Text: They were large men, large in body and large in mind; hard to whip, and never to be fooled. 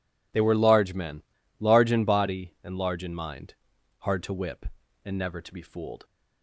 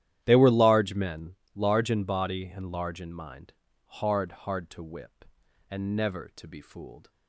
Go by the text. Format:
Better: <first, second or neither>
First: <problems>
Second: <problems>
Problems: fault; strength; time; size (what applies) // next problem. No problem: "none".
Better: first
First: none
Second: starts louder than the rest; strong; until 1.2 s; 12 dB // says "hard" twice; at 4.2 s